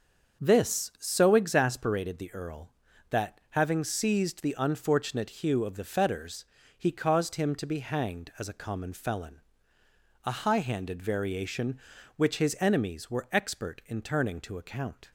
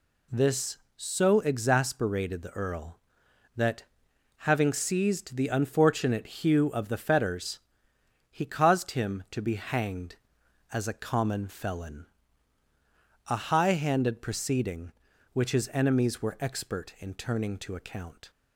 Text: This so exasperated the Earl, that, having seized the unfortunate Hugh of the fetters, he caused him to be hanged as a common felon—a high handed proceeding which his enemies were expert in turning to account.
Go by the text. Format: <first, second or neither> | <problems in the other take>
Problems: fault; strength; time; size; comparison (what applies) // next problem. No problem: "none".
second | starts louder than the rest; until 1.4 s; 6.5 dB // says "variation" for "proceeding"; at 11.0 s